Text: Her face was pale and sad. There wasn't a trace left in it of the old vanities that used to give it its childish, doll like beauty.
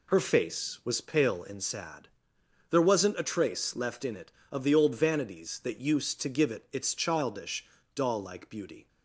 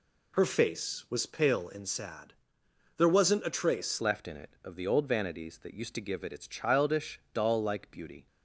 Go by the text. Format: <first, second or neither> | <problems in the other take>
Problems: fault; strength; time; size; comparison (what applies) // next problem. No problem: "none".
first | changes voice at "left"; from 4.0 s on; 4.2 s long